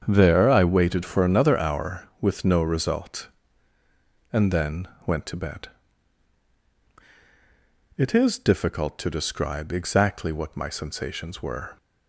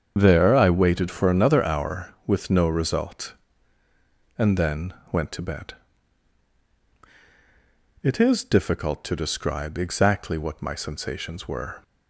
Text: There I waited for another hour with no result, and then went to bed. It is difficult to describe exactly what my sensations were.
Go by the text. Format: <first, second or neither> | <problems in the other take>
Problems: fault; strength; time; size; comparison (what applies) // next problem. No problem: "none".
first | loses the start of "There"; at 0.1 s; 85 ms // starts louder than the rest; strong; until 1.1 s; 7.5 dB; strong in the first // pauses between "then" and "went"; slight; at 4.9 s; 0.18 s long; slight in the first